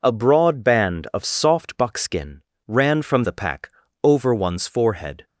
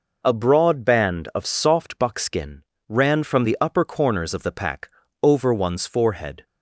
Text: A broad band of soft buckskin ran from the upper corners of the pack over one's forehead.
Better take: second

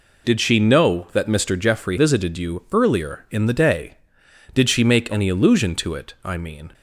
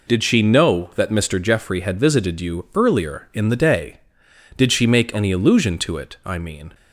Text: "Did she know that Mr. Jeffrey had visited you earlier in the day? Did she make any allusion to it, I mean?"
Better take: second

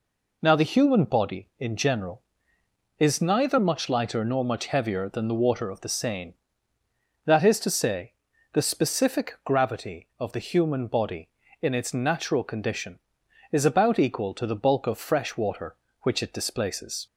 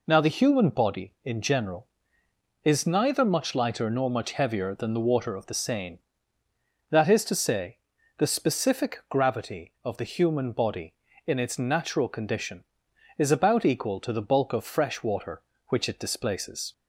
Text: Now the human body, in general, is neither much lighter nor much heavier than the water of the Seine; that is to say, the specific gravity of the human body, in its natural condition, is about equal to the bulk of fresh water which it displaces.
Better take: neither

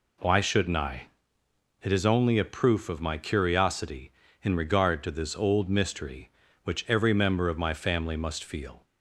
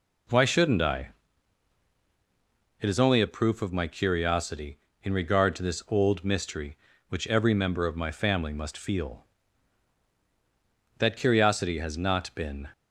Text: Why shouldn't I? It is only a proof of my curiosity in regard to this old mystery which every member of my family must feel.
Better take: first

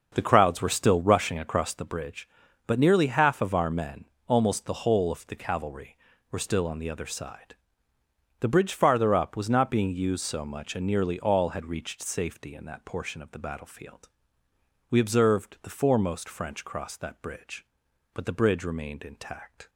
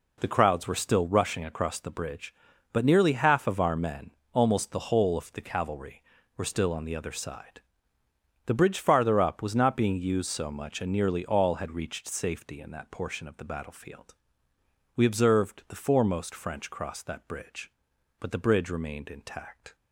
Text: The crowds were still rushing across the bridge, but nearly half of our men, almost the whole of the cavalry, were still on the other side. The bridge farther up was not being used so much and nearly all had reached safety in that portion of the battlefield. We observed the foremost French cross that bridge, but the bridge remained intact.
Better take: second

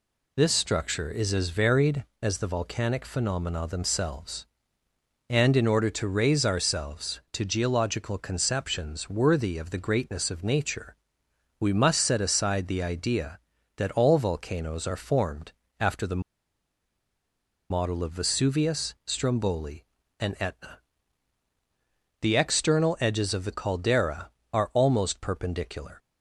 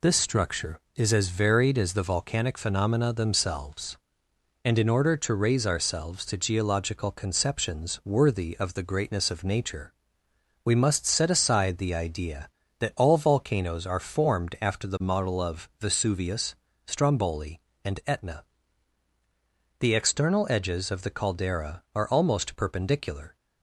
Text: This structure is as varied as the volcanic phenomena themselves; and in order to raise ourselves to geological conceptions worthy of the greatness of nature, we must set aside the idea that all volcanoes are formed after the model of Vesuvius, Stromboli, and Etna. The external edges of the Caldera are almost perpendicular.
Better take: second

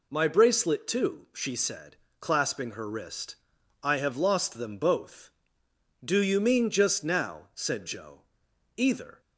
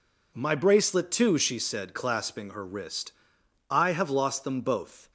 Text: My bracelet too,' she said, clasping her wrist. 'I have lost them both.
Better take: second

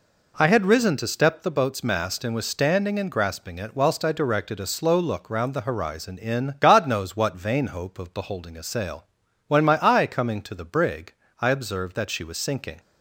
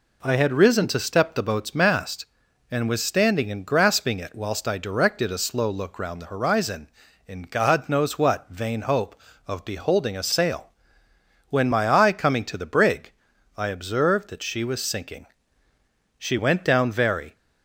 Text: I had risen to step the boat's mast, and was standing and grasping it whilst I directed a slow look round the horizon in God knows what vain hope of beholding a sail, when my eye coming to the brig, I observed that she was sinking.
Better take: first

